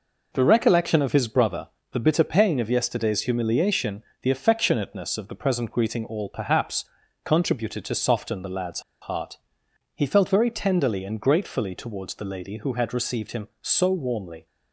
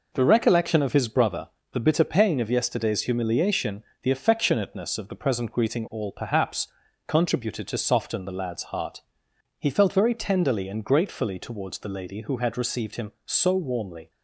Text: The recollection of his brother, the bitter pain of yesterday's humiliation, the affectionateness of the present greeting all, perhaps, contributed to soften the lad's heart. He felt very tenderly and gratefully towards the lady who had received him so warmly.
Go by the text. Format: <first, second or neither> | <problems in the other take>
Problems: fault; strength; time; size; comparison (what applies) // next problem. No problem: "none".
second | pauses between "lad's" and "heart"; slight; at 8.8 s; 0.20 s long